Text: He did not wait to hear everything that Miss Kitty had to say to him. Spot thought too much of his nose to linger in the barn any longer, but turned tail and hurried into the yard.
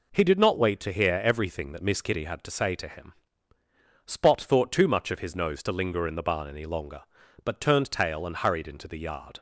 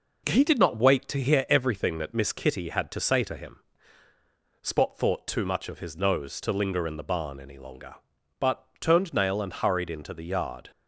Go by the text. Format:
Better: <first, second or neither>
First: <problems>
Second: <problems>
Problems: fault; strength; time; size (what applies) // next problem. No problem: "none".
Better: first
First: none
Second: pauses between "but" and "turned"; slight; at 8.6 s; 0.16 s long // says "nail" for "tail"; at 9.1 s